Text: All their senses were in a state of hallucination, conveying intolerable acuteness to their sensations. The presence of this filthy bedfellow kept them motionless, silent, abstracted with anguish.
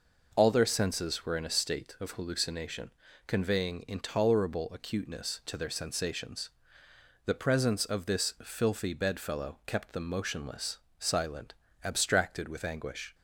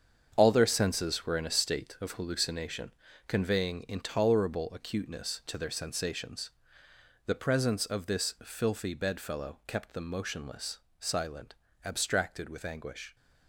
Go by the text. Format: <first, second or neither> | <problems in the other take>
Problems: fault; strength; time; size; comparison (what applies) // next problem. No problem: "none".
first | gets quieter; strong; throughout; 9 dB